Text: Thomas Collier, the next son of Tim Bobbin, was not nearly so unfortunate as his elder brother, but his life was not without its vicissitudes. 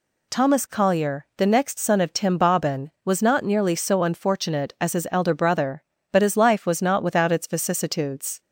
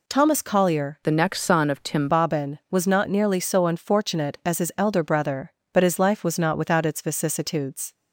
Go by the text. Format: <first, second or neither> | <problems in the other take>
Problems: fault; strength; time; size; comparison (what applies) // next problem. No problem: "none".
first | changes voice from "the" to "Tim"; from 1.0 to 2.0 s; 1.0 s long